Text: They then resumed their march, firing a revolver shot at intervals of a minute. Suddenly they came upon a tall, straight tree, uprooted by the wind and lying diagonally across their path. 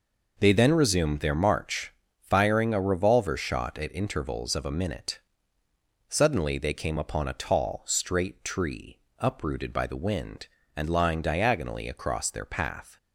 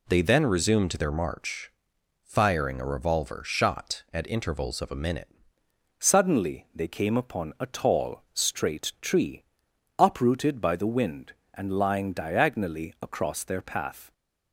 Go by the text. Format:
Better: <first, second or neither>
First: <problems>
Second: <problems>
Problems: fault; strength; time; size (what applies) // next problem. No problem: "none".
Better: first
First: none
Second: changes voice at "Suddenly"; from 5.9 s on; 8.2 s long